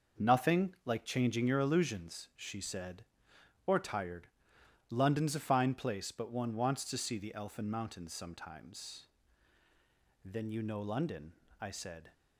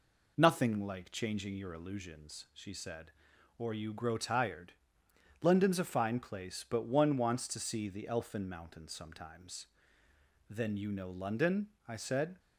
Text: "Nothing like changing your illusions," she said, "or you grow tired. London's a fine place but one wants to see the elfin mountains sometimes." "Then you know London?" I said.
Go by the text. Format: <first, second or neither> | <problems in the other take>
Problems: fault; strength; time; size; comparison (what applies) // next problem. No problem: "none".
second | skips "you grow"; at 3.7 s